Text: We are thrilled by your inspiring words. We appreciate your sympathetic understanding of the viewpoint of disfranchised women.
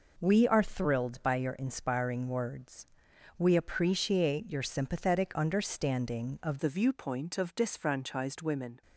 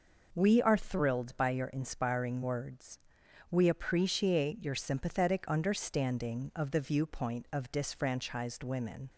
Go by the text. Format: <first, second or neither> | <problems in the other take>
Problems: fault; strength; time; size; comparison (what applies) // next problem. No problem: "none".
second | changes voice at "the"; from 6.5 s on; 2.3 s long